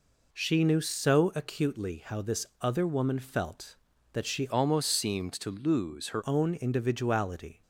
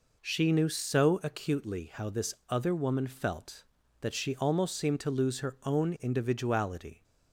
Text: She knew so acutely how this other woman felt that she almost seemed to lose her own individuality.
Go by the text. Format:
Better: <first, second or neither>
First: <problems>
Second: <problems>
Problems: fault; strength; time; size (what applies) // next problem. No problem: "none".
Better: second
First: changes voice from "almost" to "her"; from 4.4 to 6.2 s; 1.8 s long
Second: none